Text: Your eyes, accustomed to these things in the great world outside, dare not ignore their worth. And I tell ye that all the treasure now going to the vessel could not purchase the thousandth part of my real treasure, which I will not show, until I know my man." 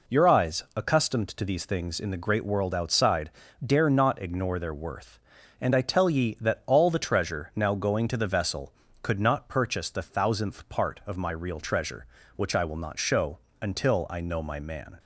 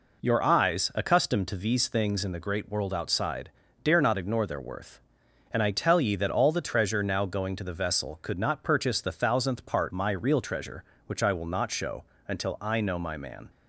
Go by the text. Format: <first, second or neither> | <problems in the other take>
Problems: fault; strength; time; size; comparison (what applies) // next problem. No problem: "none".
first | skips "of"; at 9.9 s